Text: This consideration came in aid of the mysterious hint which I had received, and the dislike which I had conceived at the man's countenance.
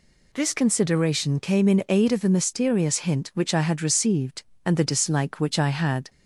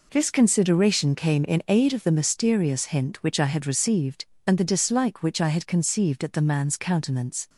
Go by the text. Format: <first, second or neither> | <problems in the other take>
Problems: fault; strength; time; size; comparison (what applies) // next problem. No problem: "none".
second | stops before "conceived at the man's countenance"; at 6.0 s